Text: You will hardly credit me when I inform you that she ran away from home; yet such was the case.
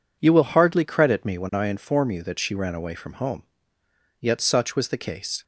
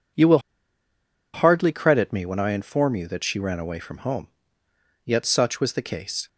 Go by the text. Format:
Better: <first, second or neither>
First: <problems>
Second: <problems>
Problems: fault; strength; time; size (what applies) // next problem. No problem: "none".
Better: first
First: none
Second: pauses between "will" and "hardly"; noticeable; at 0.3 s; 0.94 s long